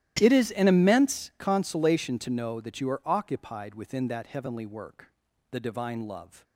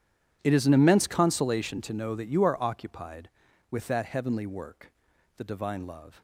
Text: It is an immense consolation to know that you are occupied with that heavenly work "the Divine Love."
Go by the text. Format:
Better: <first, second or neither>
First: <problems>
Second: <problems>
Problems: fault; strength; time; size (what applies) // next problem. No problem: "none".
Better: second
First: starts louder than the rest; strong; until 1.2 s; 13.5 dB // says "within" for "with"; at 3.7 s // pauses between "work" and "the"; at 5.1 s; 0.40 s long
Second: pauses between "work" and "the"; noticeable; at 4.8 s; 0.46 s long